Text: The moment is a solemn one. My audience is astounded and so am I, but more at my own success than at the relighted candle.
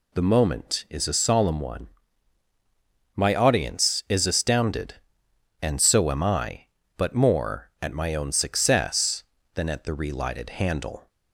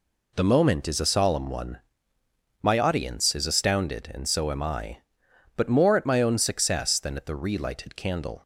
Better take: second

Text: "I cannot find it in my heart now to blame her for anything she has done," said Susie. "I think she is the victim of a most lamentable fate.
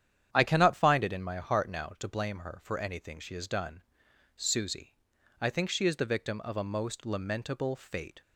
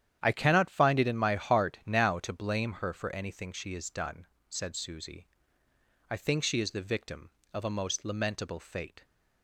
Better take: second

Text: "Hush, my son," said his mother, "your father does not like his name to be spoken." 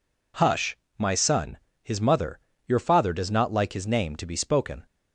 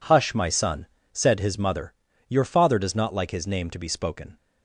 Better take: second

